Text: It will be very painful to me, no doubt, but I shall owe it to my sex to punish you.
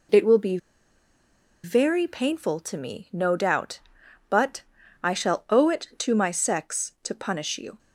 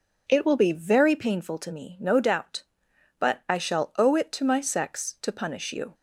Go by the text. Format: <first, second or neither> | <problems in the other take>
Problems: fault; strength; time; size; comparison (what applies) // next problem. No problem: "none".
second | pauses between "be" and "very"; at 0.5 s; 1.0 s long // pauses between "but" and "I"; at 4.6 s; 0.42 s long